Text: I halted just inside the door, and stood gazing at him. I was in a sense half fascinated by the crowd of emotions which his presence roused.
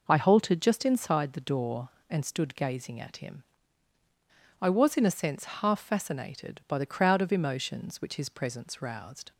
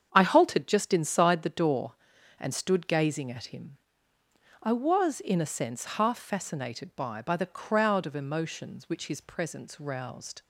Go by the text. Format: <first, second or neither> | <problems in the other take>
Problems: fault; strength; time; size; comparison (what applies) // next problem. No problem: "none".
first | starts louder than the rest; strong; until 1.1 s; 7.5 dB // says "by" twice; at 7.2 s